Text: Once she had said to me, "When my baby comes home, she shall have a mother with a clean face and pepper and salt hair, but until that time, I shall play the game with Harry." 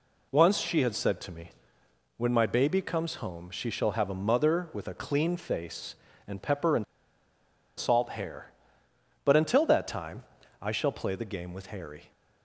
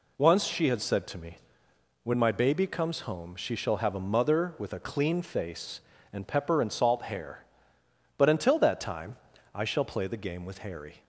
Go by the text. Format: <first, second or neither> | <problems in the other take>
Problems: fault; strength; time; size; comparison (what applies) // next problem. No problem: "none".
second | pauses between "and" and "salt"; noticeable; at 6.8 s; 0.94 s long